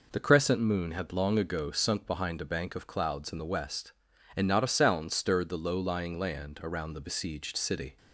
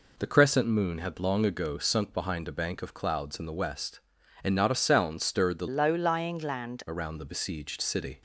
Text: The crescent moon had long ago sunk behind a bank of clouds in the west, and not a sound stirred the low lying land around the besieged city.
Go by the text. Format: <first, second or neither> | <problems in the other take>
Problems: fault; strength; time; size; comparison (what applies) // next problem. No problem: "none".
first | changes voice from "low" to "land"; from 5.6 to 6.8 s; 1.2 s long